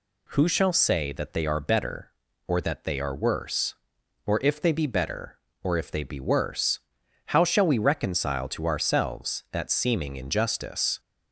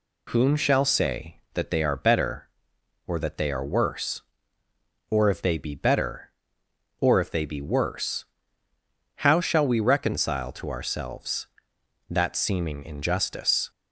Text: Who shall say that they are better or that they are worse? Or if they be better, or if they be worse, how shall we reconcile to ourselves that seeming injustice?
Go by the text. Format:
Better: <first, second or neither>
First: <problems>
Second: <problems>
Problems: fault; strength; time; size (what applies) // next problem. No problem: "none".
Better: first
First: none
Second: says "Whom" for "Who"; at 0.3 s